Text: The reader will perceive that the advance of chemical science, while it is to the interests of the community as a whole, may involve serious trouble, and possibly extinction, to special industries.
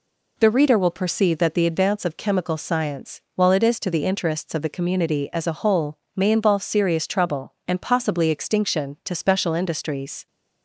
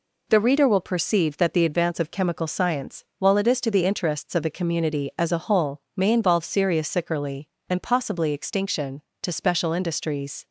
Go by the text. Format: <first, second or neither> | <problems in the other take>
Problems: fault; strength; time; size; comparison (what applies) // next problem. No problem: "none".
first | says "sickerly" for "trouble"; at 6.8 s